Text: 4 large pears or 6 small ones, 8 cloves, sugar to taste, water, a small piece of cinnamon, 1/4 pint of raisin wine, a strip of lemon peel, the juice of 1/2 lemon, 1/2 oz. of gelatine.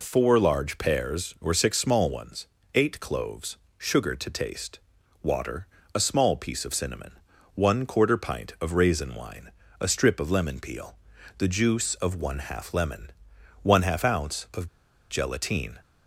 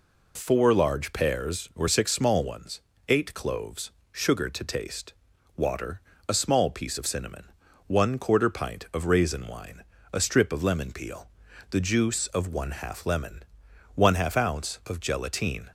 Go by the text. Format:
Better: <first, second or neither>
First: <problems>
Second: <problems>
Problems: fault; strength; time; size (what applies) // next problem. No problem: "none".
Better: second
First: pauses between "of" and "gelatine"; at 14.6 s; 0.44 s long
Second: none